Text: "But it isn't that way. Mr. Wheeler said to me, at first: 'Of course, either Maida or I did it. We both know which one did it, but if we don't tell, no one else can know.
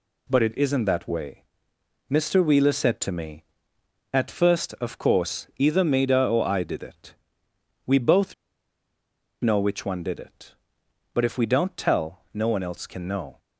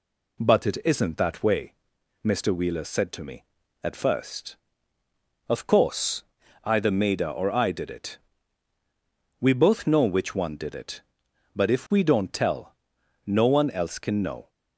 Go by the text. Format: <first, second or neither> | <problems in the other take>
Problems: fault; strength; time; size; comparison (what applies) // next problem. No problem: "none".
second | pauses between "both" and "know"; at 8.3 s; 1.0 s long